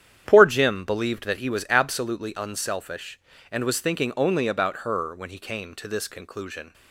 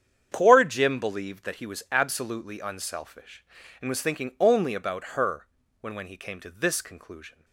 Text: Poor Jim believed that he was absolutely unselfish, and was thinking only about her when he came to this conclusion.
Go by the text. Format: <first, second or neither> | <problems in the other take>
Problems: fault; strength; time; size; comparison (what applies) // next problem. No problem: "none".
first | starts louder than the rest; strong; until 1.3 s; 8.5 dB; strong in the first // pauses between "her" and "when"; slight; at 5.4 s; 0.34 s long // says "when" twice; at 5.9 s